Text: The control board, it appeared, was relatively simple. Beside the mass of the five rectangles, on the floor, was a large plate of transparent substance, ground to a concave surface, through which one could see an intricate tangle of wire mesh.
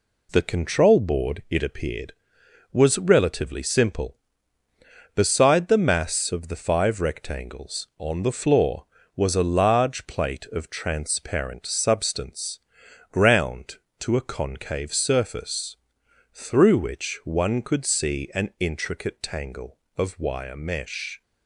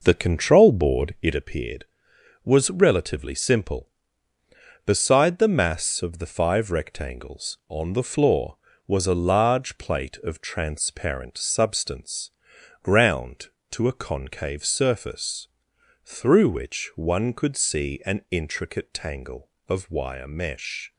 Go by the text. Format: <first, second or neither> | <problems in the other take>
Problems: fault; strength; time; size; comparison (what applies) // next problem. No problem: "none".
first | starts louder than the rest; noticeable; until 1.4 s; 5.5 dB